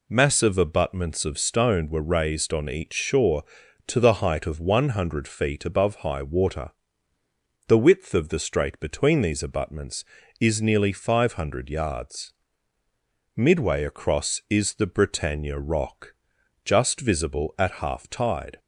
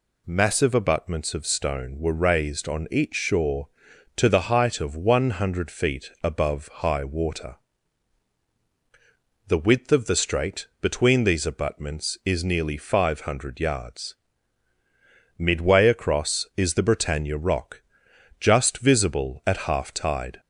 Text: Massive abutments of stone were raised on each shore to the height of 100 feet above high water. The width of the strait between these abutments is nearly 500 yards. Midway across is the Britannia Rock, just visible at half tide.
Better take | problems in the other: neither | none

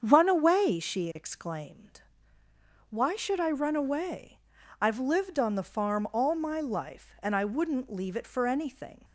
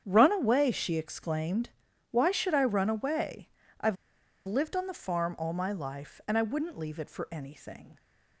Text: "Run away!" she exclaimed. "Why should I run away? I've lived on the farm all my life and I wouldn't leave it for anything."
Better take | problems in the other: first | starts louder than the rest; strong; until 1.0 s; 8.5 dB; strong in the first // pauses between "I've" and "lived"; noticeable; at 3.9 s; 0.52 s long

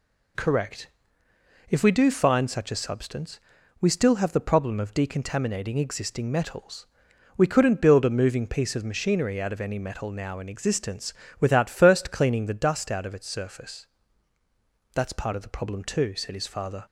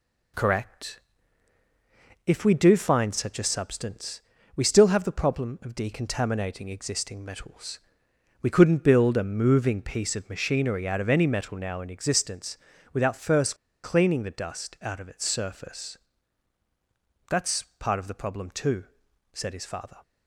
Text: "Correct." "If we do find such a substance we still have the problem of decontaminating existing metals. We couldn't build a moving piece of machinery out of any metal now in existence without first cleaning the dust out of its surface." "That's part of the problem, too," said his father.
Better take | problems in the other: first | pauses between "substance" and "we"; slight; at 4.2 s; 0.36 s long; also in the first // pauses between "existence" and "without"; slight; at 12.5 s; 0.36 s long; slight in the first // pauses between "first" and "cleaning"; slight; at 13.5 s; 0.27 s long // pauses between "That's" and "part"; slight; at 17.6 s; 0.16 s long

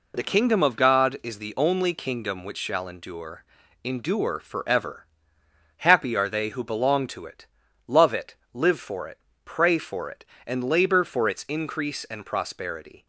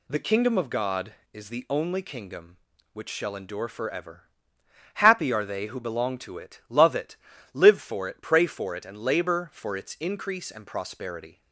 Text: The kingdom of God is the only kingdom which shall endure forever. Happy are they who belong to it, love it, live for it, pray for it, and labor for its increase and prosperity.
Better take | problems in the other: second | says "endure" twice; at 3.8 s

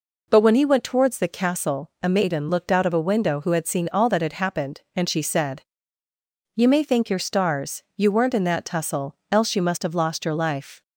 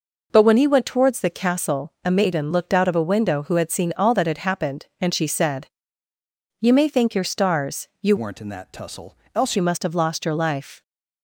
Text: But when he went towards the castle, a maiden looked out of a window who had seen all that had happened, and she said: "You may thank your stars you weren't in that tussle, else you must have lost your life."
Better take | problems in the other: first | changes voice from "weren't" to "else"; from 8.1 to 9.5 s; 1.4 s long

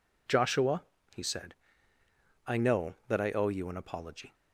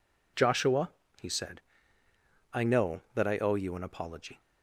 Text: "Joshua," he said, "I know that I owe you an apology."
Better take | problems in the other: neither | none

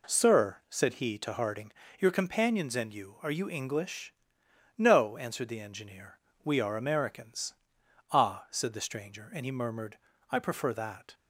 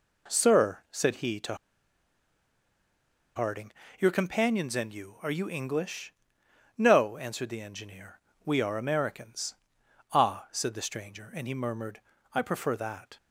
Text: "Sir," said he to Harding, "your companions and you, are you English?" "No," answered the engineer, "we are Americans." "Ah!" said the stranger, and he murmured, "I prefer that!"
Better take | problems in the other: first | pauses between "to" and "Harding"; strong; at 1.5 s; 1.8 s long

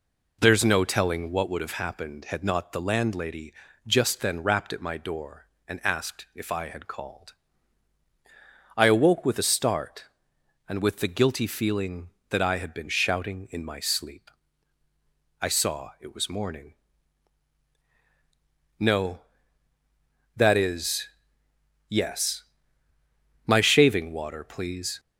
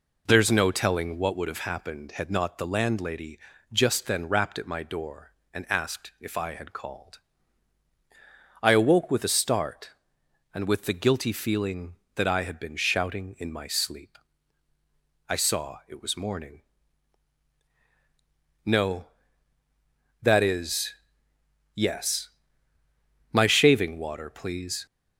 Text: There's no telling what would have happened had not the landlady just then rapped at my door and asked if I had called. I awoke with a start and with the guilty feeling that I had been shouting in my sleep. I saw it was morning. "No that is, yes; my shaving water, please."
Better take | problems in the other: neither | pauses between "landlady" and "just"; slight; the same in both

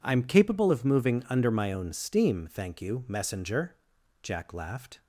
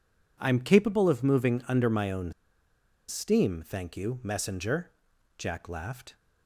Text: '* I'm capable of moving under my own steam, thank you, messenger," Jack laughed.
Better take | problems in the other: first | pauses between "own" and "steam"; noticeable; at 2.3 s; 0.77 s long

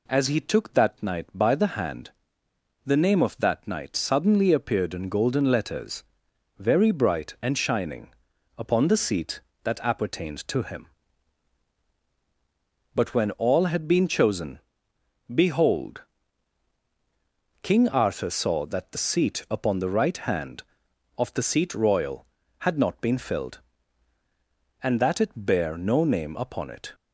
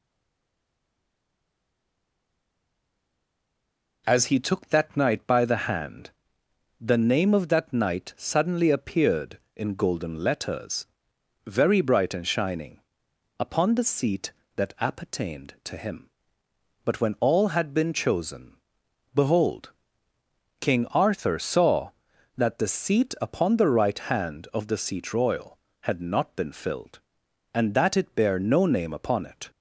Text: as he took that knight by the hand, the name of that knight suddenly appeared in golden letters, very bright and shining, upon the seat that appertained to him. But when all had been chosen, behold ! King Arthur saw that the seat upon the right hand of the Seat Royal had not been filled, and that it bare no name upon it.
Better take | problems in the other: first | stays silent before the first word; strong; until 4.0 s; 4.0 s long

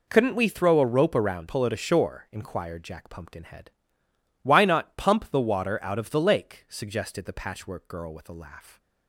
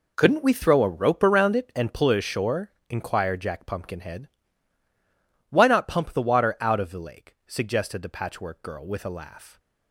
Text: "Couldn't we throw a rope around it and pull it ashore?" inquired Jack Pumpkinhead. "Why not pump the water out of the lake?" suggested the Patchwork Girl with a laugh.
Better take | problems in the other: second | skips "it and"; at 1.4 s

